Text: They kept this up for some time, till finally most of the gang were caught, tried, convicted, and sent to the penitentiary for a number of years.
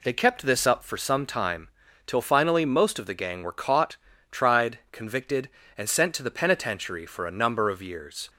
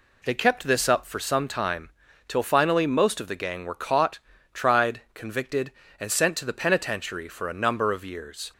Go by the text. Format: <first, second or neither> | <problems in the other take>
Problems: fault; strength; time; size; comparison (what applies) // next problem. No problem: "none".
neither | none